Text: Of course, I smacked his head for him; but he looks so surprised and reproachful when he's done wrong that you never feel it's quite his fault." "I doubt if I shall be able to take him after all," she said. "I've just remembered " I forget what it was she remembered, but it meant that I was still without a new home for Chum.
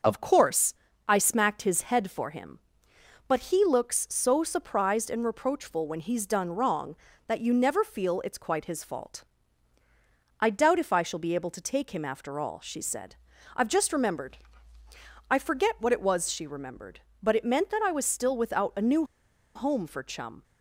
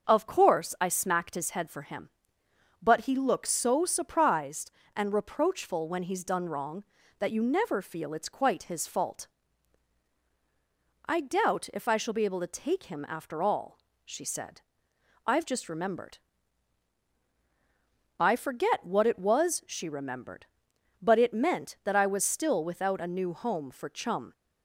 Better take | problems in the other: second | starts louder than the rest; until 1.3 s; 6 dB; also in the second // pauses between "new" and "home"; noticeable; at 19.0 s; 0.51 s long

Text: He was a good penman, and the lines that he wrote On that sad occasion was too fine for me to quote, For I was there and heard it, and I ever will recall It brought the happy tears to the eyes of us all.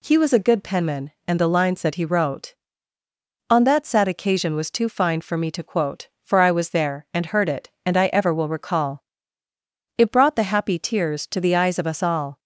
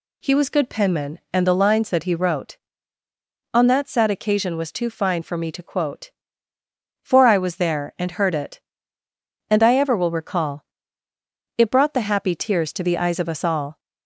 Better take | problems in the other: first | skips "a"; at 0.5 s // pauses between "recall" and "It"; noticeable; at 10.6 s; 0.94 s long; noticeable in the first

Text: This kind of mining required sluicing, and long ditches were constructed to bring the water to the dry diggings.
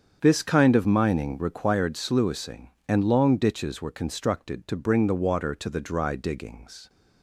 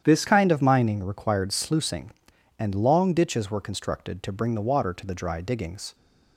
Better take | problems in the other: first | starts louder than the rest; strong; until 1.0 s; 9 dB; strong in the first // changes voice at "kind"; from 0.2 s on; 5.7 s long

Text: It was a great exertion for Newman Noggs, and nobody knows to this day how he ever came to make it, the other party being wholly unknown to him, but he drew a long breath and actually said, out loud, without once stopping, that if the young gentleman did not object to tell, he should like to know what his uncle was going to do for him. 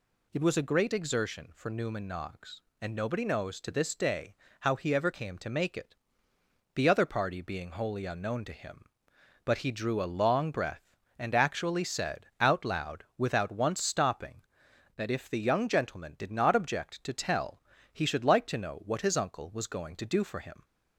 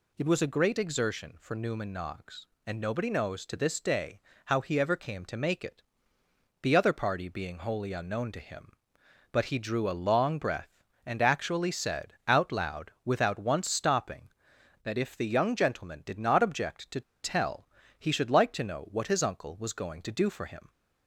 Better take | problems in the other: first | pauses between "day" and "how"; slight; at 4.1 s; 0.26 s long; slight in the first // pauses between "to" and "tell"; slight; at 17.0 s; 0.21 s long

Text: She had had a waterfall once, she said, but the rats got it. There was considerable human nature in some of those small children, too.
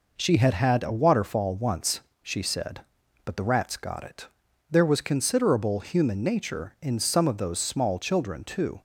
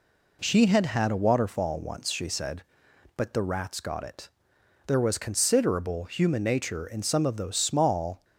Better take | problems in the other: first | stops before "children too"; at 8.2 s

